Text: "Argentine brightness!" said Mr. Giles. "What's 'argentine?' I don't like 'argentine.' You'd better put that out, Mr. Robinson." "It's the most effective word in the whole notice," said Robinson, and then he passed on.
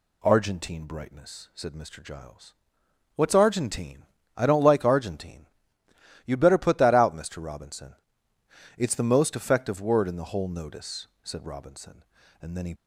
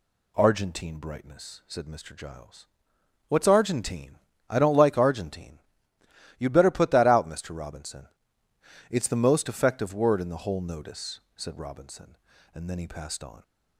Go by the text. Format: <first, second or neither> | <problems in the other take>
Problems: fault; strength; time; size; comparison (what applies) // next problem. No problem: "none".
second | stops before "passed on"; at 12.7 s